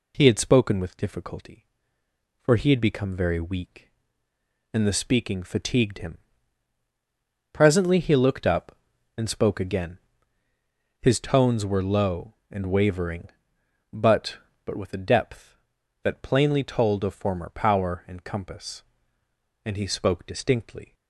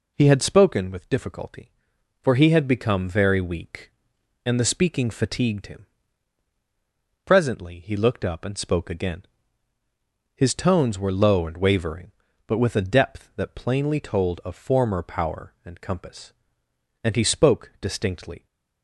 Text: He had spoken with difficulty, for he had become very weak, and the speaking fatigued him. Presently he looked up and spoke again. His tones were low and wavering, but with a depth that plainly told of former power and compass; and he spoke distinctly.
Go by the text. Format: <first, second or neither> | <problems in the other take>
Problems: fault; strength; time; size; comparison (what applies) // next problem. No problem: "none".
second | says "but" twice; at 14.6 s